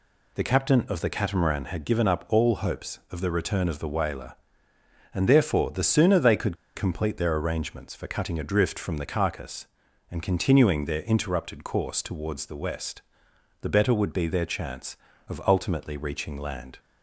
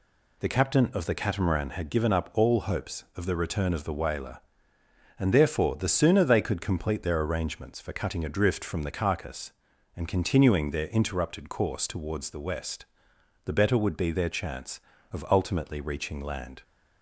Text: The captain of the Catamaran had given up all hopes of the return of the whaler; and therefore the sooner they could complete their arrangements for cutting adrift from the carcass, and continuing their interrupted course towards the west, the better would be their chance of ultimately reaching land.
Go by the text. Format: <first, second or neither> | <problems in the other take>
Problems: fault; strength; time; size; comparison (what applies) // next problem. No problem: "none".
second | pauses between "could" and "complete"; slight; at 6.5 s; 0.20 s long